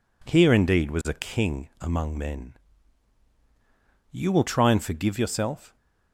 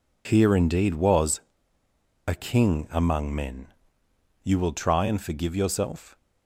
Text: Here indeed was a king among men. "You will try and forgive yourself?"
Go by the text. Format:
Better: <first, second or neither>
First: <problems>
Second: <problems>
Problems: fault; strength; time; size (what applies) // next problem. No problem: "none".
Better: first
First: none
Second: pauses between "was" and "a"; noticeable; at 1.4 s; 0.87 s long